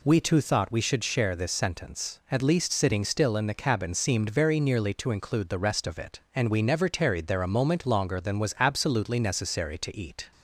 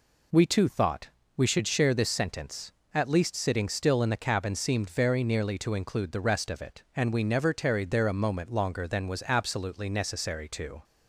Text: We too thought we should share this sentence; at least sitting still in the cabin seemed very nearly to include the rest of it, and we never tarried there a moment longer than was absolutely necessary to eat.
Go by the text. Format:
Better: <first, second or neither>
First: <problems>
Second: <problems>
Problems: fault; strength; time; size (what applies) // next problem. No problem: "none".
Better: first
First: none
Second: pauses between "thought" and "we"; slight; at 1.0 s; 0.28 s long // stops before "eat"; at 10.8 s